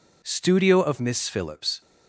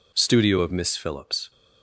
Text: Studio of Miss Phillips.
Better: neither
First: none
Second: none

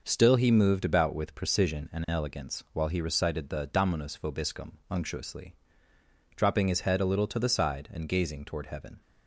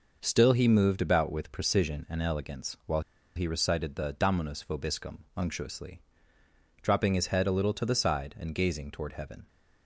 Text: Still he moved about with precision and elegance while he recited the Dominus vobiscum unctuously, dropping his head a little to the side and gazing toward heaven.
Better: first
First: none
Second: pauses between "while" and "he"; slight; at 2.9 s; 0.36 s long

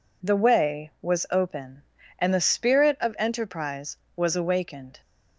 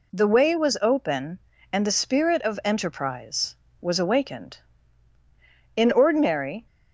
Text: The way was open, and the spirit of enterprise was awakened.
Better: first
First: none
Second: goes on to say "In ordinary"; noticeable; from 5.7 s on; 0.90 s long

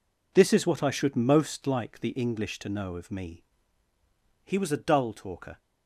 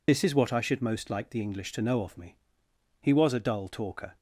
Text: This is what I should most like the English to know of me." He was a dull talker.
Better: first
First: none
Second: loses the start of "This"; at 0.0 s; 75 ms

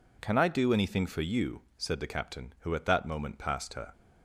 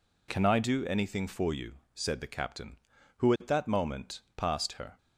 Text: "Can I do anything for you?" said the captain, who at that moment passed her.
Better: neither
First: none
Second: none

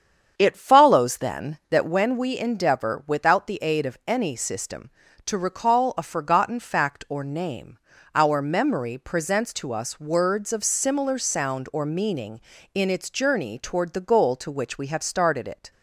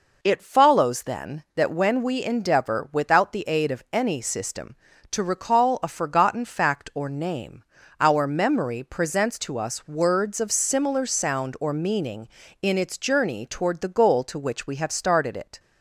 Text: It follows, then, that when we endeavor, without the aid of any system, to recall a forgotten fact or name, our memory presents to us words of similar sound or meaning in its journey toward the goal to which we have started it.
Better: second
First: starts louder than the rest; strong; until 2.0 s; 7.5 dB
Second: none

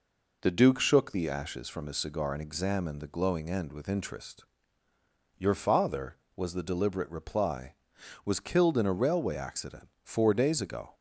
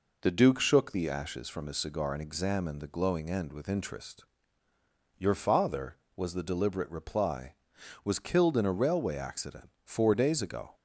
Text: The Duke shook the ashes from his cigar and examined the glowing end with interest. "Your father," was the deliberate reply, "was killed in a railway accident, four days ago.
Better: neither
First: none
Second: none

